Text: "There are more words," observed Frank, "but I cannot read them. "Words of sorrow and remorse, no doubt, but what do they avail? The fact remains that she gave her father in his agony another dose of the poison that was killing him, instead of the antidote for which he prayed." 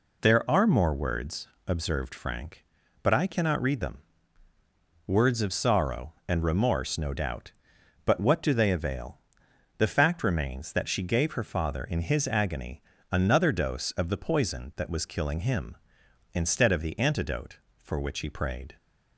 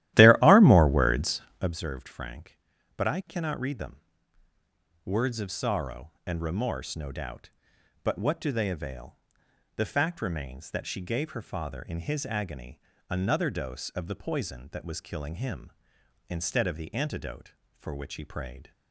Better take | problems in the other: first | starts louder than the rest; strong; until 1.7 s; 14 dB // pauses between "agony" and "another"; slight; at 12.7 s; 0.28 s long; slight in the first

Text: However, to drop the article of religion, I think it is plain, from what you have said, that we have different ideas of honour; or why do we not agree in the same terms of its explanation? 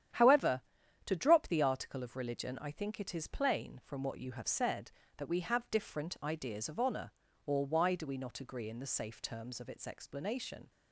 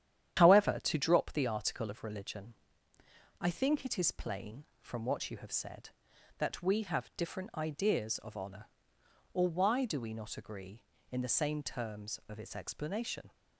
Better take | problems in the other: second | starts louder than the rest; strong; until 1.5 s; 10 dB; strong in the second // says "safe" for "same"; at 8.8 s

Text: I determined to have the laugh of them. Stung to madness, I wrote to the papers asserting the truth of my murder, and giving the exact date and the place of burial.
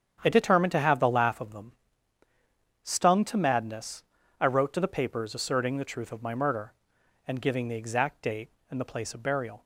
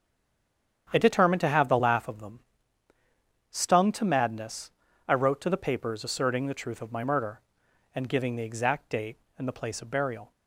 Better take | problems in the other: first | stays silent before the first word; slight; until 0.8 s; 0.8 s long // starts louder than the rest; strong; until 1.9 s; 8.5 dB; strong in the first

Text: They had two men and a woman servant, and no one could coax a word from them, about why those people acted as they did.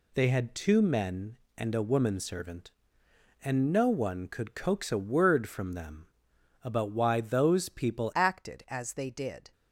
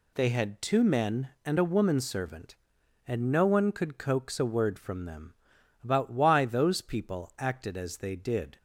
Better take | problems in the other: second | changes voice at "acted"; from 8.1 s on; 1.4 s long

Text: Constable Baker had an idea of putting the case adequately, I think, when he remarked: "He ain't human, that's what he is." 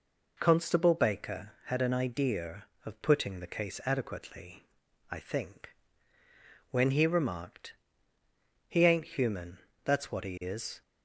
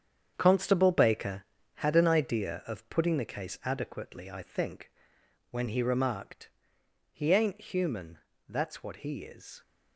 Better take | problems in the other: first | gets quieter; strong; throughout; 10 dB

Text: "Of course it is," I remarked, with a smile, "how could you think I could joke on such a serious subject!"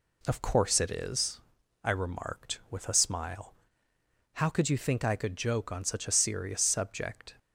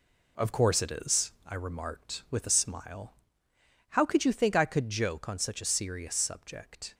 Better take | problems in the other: first | gets quieter; noticeable; throughout; 5.5 dB

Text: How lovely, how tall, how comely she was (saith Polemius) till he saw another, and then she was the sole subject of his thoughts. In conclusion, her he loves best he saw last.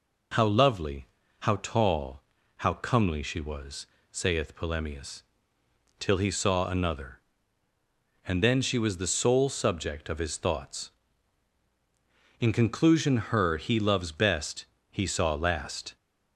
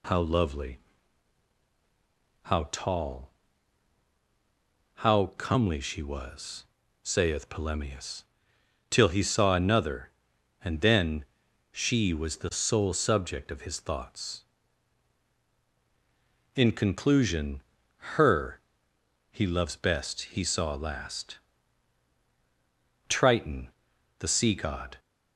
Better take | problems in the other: first | pauses between "then" and "she"; noticeable; at 11.2 s; 0.46 s long // pauses between "her" and "he"; noticeable; at 18.6 s; 0.68 s long // pauses between "best" and "he"; slight; at 20.2 s; 0.16 s long; slight in the first // goes on to say "Triton the sea god"; strong; from 23.0 s on; 1.9 s long

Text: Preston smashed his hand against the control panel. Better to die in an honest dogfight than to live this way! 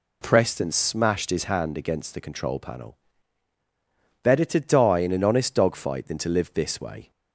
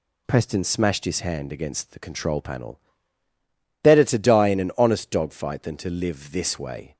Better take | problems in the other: neither | none

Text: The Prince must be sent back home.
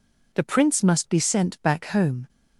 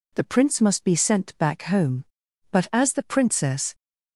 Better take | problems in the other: first | goes on to say "But as the Princess"; noticeable; from 2.5 s on; 1.2 s long

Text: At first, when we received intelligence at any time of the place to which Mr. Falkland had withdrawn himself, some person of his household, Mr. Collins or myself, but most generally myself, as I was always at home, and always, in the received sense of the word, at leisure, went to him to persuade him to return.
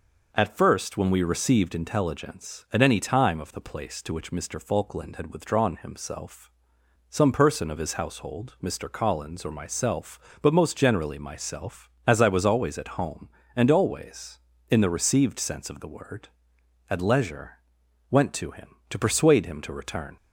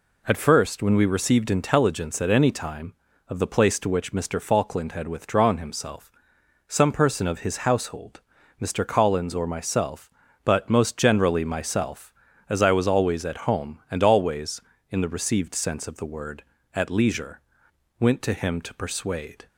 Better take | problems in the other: first | stops before "him to return"; at 19.4 s

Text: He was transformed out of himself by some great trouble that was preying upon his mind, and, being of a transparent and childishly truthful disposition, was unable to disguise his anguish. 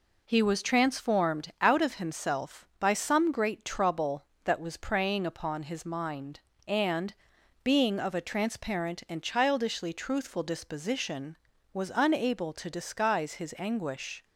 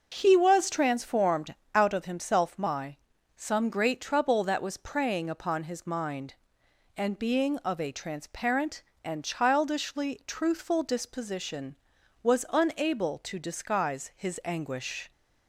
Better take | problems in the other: first | pauses between "transformed" and "out"; slight; at 1.5 s; 0.18 s long // says "my" for "by"; at 2.5 s

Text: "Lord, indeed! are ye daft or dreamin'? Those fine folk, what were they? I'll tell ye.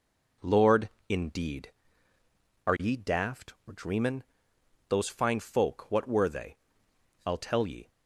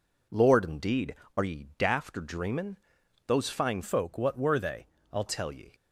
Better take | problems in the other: first | changes voice from "folk" to "I'll"; from 3.8 to 5.2 s; 1.4 s long

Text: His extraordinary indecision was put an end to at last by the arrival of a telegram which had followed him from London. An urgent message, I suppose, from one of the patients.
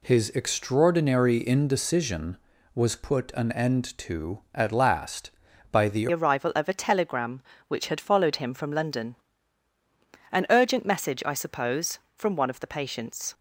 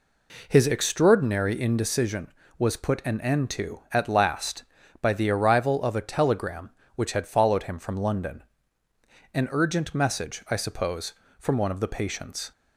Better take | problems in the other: second | changes voice at "arrival"; from 6.1 s on; 7.2 s long

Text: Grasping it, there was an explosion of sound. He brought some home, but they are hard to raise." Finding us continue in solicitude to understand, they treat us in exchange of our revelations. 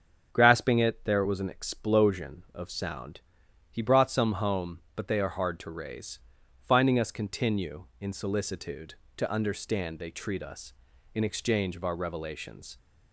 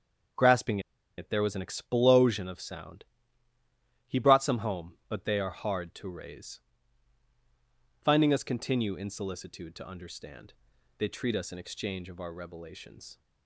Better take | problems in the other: first | starts louder than the rest; strong; until 1.7 s; 7.5 dB; strong in the first // pauses between "Grasping" and "it"; at 0.7 s; 0.38 s long

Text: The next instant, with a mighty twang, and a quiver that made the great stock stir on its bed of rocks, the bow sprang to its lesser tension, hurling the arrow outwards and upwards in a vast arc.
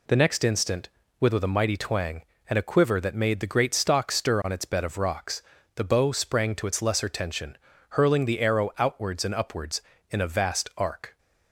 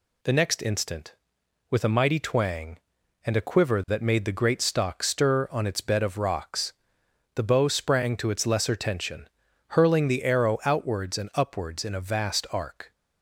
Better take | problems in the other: second | says "with" twice; at 1.3 s

